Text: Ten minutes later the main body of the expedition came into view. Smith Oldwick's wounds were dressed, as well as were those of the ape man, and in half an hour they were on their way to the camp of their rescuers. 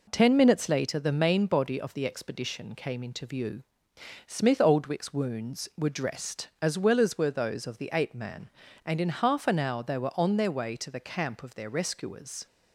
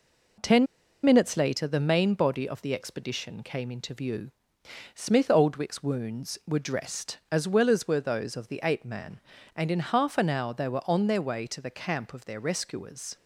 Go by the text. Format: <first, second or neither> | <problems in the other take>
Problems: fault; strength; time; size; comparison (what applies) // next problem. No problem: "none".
first | pauses between "Ten" and "minutes"; at 0.6 s; 0.38 s long